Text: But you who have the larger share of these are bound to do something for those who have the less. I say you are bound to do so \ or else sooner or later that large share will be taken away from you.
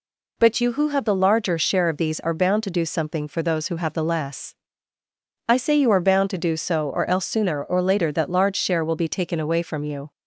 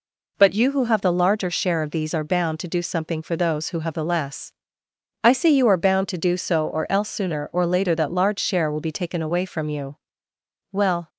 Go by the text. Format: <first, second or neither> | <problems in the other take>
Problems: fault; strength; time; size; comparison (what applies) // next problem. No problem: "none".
first | goes on to say "Well"; slight; from 10.7 s on; 0.36 s long